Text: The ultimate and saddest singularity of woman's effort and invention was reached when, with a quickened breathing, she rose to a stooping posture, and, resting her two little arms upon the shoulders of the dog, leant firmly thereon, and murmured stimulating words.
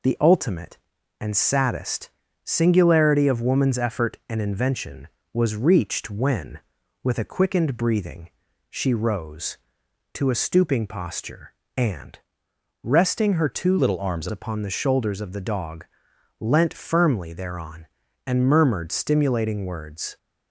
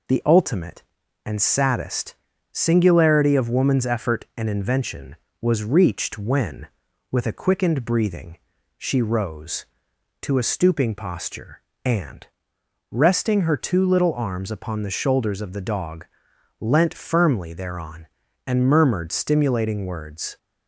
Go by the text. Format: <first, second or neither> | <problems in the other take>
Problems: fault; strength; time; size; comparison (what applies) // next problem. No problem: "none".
second | pauses between "saddest" and "singularity"; slight; at 2.0 s; 0.34 s long; also in the second // changes voice from "little" to "arms"; from 13.7 to 14.2 s; 0.5 s long